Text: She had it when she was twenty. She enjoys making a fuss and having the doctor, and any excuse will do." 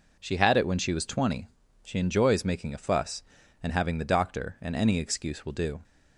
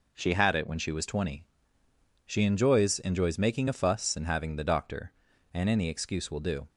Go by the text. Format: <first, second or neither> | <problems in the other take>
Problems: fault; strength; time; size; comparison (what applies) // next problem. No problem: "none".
first | says "enjoys" twice; at 2.9 s